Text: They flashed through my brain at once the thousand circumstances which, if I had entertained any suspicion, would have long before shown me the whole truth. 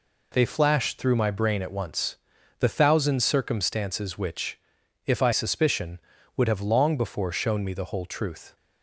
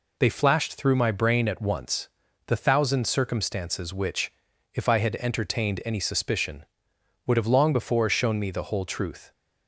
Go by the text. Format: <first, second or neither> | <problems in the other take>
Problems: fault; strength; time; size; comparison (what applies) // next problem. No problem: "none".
second | pauses between "once" and "the"; at 2.1 s; 0.42 s long; also in the second // skips "had entertained any"; at 5.3 s